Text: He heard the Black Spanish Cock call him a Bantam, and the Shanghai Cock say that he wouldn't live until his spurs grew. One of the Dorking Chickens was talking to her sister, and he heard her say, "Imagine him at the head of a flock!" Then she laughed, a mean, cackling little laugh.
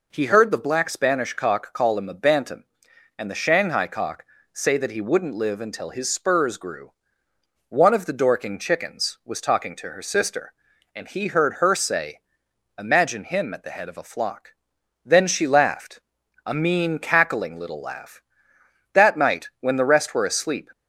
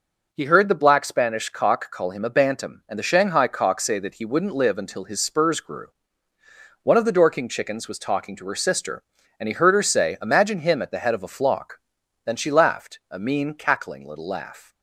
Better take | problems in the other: second | pauses between "Cock" and "say"; slight; at 4.2 s; 0.28 s long // goes on to say "That night when the rest were asleep"; strong; from 18.9 s on; 1.8 s long

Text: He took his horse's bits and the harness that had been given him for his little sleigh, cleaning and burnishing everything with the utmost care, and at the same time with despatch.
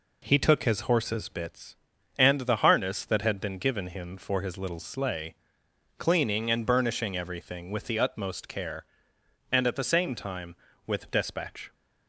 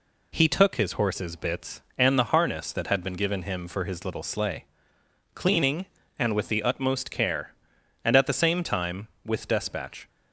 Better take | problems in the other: first | skips "burnishing everything"; at 6.3 s

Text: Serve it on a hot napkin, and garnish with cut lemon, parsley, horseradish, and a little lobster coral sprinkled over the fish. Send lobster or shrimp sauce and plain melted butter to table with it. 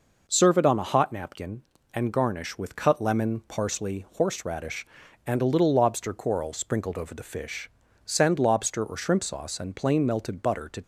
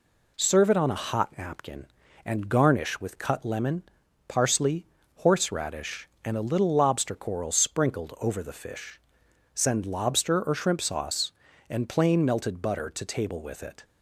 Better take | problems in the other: second | stops before "table with it"; at 10.8 s

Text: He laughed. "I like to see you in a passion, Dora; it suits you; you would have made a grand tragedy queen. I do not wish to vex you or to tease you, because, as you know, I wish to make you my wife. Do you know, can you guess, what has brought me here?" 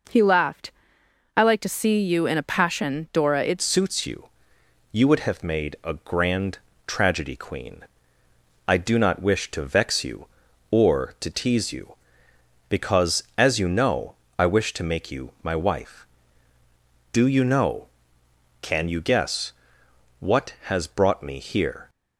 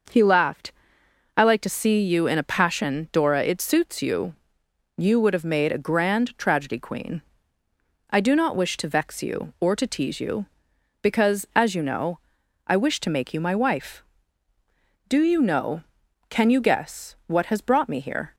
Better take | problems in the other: second | changes voice at "suits"; from 3.6 s on; 18.2 s long // pauses between "grand" and "tragedy"; slight; at 6.5 s; 0.28 s long

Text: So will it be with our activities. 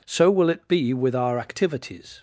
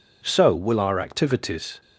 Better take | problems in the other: first | skips "it be with"; at 0.7 s

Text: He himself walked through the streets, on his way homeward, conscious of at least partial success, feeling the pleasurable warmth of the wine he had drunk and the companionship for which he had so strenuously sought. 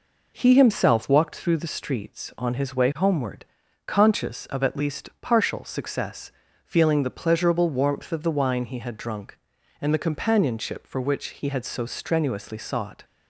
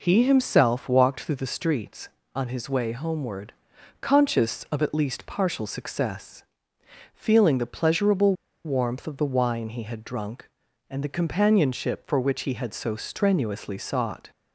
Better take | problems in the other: first | pauses between "pleasurable" and "warmth"; slight; at 8.3 s; 0.31 s long

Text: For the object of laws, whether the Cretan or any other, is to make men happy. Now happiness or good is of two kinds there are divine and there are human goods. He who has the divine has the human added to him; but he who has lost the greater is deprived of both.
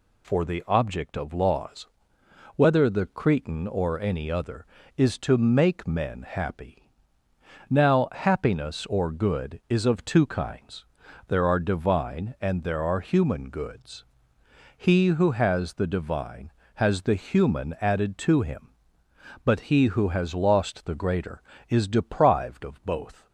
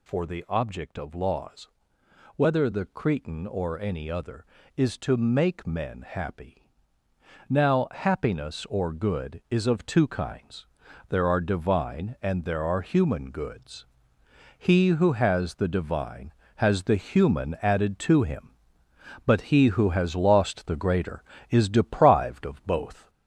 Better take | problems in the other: first | gets louder; noticeable; throughout; 4.5 dB // pauses between "kinds" and "there"; at 10.6 s; 0.42 s long; also in the first

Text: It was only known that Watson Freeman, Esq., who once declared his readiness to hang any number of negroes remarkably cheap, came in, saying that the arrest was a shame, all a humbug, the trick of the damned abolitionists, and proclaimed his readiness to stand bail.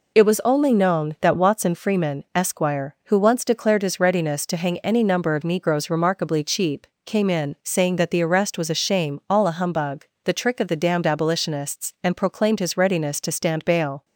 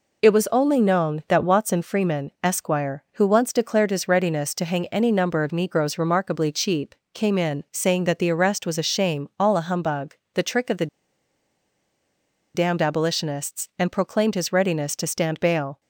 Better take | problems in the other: first | pauses between "the" and "damned"; strong; at 10.8 s; 1.6 s long

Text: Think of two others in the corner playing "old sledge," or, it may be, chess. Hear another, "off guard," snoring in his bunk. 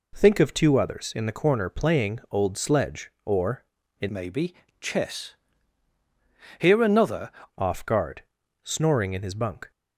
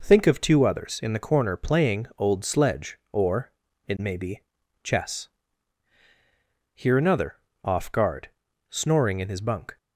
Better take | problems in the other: second | changes voice from "may" to "another"; from 4.0 to 7.3 s; 3.3 s long

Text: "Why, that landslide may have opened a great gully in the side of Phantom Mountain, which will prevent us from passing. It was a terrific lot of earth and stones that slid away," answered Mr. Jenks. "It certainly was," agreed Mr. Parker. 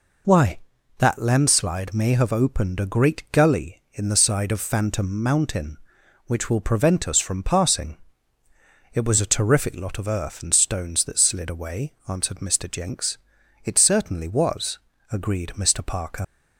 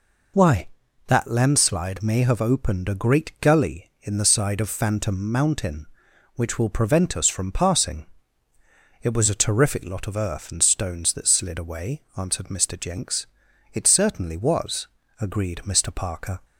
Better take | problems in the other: second | leaves "Parker" unfinished; at 16.2 s; 110 ms

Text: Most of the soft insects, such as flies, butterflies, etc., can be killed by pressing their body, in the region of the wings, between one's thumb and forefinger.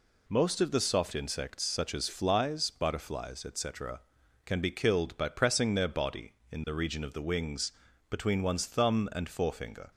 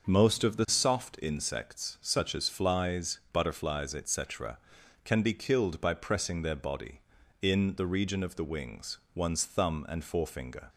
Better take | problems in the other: first | starts louder than the rest; noticeable; until 1.1 s; 6 dB // skips "between"; at 9.0 s

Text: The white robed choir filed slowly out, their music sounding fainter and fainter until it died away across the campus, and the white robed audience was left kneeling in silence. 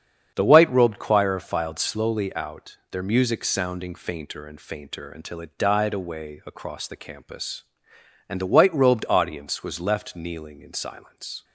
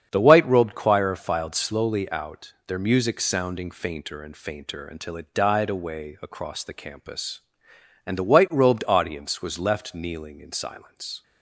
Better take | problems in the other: neither | starts louder than the rest; strong; the same in both

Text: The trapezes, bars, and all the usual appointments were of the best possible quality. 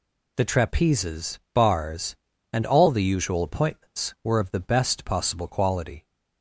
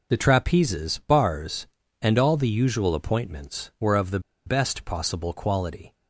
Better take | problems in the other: first | pauses between "the" and "best"; slight; at 4.1 s; 0.26 s long

